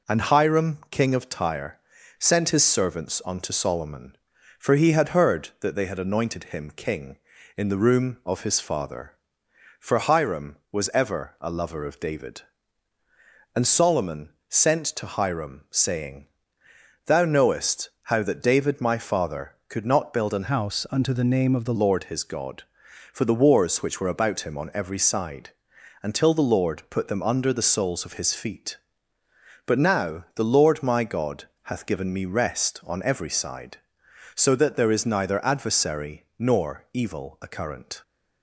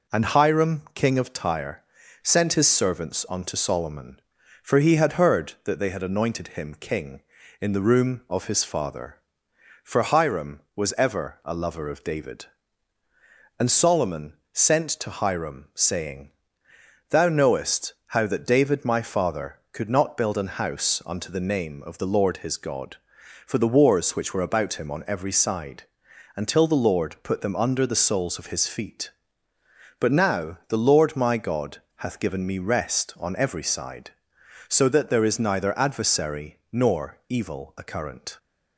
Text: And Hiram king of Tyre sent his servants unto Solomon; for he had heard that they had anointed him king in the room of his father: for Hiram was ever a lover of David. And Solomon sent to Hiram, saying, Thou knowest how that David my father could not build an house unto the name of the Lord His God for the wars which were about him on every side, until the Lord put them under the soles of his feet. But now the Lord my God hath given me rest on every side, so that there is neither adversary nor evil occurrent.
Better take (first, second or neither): second